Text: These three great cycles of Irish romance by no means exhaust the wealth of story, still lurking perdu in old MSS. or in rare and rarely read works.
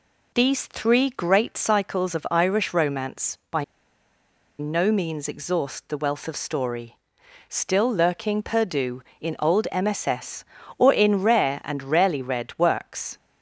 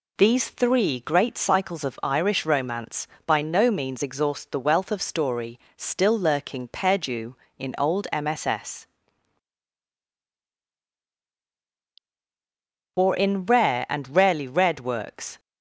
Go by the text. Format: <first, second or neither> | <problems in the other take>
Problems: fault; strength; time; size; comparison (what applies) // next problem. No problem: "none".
second | pauses between "by" and "no"; noticeable; at 3.6 s; 0.94 s long